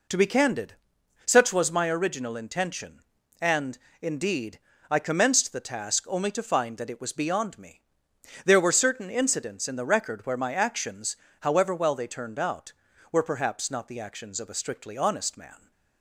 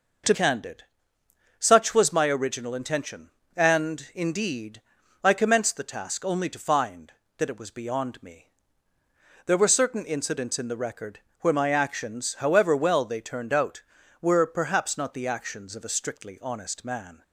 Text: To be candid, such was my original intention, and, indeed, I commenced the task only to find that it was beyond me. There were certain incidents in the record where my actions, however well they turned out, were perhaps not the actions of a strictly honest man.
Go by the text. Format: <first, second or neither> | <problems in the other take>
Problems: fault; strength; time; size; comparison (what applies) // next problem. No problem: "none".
first | skips "be"; at 0.3 s // pauses between "record" and "where"; slight; at 11.2 s; 0.22 s long